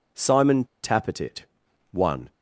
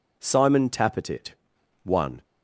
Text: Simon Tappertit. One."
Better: second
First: pauses between "Simon" and "Tappertit"; slight; at 0.6 s; 0.18 s long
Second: none

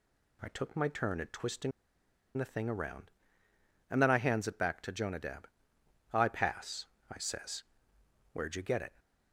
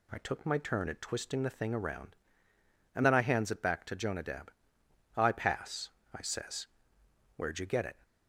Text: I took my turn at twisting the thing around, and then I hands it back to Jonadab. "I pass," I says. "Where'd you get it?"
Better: second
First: pauses between "twisting" and "the"; noticeable; at 1.7 s; 0.66 s long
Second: none

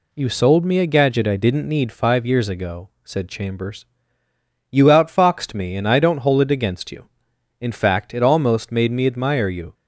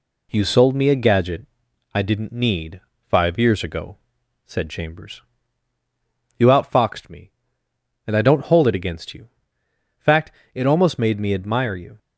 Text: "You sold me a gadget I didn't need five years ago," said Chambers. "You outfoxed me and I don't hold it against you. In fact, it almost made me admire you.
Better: first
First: none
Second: pauses between "gadget" and "I"; noticeable; at 1.4 s; 0.46 s long // pauses between "need" and "five"; slight; at 2.8 s; 0.28 s long // skips "In"; at 9.6 s

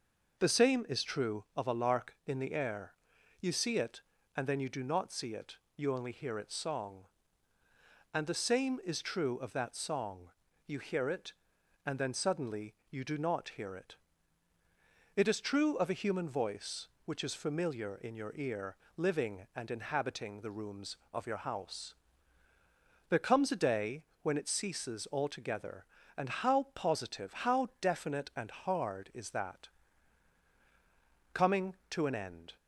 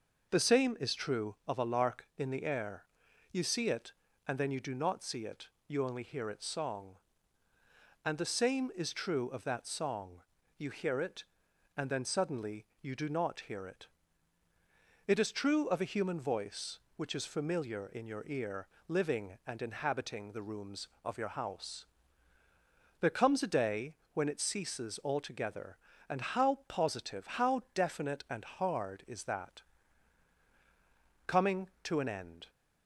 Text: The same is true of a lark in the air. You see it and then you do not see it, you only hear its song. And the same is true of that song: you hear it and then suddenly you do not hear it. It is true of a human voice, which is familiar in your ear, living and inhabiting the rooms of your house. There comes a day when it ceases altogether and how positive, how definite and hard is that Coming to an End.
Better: neither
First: pauses between "suddenly" and "you"; slight; at 12.7 s; 0.16 s long // pauses between "day" and "when"; slight; at 24.0 s; 0.18 s long // pauses between "that" and "Coming"; strong; at 29.6 s; 1.6 s long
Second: pauses between "suddenly" and "you"; slight; at 12.6 s; 0.16 s long // pauses between "day" and "when"; slight; at 23.9 s; 0.18 s long // pauses between "that" and "Coming"; strong; at 29.6 s; 1.6 s long

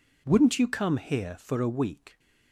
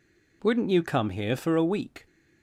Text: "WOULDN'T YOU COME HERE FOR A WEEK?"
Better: neither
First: none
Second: none

